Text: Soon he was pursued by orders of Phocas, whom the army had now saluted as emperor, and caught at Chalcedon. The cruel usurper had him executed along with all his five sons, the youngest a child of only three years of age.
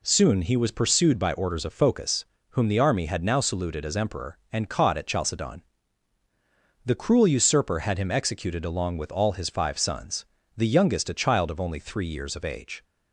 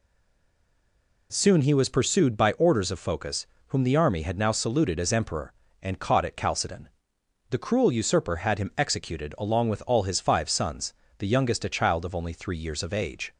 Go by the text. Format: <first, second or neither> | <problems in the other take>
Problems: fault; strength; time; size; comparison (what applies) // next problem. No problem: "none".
first | stays silent before the first word; noticeable; until 1.2 s; 1.2 s long